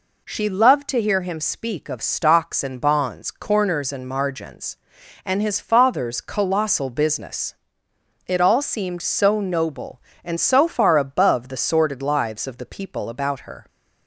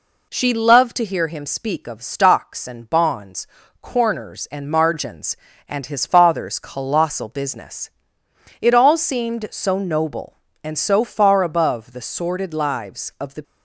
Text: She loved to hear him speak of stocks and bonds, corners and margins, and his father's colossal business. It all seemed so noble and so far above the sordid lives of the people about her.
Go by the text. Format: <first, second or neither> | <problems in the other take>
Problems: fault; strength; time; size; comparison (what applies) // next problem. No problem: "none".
first | stops before "people about her"; at 13.4 s